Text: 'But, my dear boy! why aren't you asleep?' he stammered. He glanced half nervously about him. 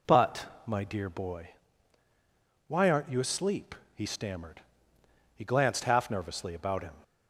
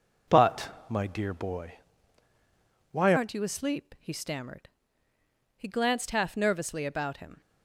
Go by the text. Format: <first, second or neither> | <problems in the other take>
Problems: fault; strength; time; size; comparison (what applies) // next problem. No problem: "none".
first | changes voice at "aren't"; from 3.1 s on; 4.3 s long